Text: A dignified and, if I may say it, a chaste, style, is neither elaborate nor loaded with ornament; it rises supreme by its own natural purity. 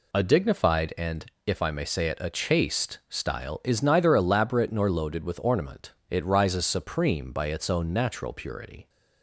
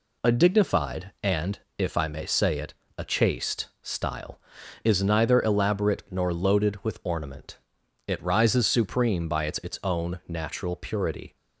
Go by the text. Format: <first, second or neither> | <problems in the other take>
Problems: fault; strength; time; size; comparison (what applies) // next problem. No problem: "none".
first | says "its" twice; at 9.5 s